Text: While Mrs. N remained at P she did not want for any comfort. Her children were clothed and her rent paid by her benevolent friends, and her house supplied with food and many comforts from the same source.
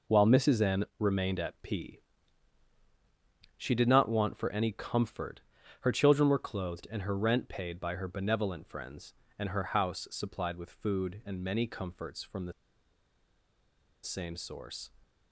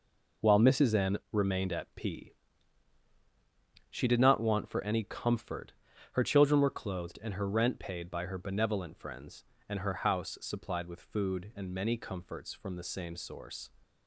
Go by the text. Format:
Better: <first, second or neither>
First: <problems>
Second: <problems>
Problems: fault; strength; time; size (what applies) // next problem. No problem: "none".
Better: second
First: pauses between "P" and "she"; strong; at 1.9 s; 1.5 s long // pauses between "the" and "same"; strong; at 12.5 s; 1.5 s long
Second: pauses between "P" and "she"; strong; at 2.3 s; 1.5 s long